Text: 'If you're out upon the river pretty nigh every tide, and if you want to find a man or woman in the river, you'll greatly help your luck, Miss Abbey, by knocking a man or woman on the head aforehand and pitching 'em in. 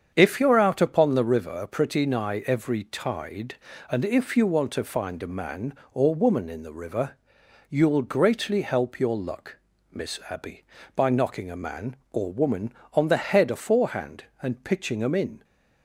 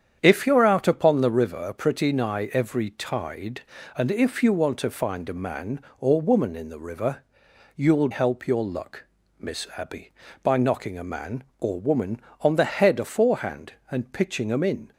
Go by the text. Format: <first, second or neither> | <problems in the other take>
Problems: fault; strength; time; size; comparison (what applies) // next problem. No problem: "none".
first | starts louder than the rest; strong; until 1.2 s; 8.5 dB; strong in the first // skips "greatly"; at 8.0 s